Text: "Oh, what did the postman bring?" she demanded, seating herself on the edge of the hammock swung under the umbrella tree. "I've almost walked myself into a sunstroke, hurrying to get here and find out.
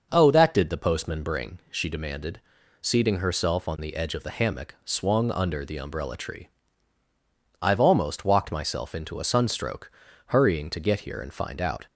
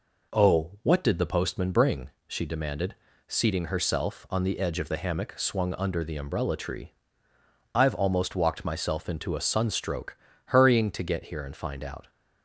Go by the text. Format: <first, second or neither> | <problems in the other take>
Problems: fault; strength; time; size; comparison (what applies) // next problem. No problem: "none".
second | starts louder than the rest; noticeable; until 1.1 s; 6 dB // says "that" for "what"; at 0.3 s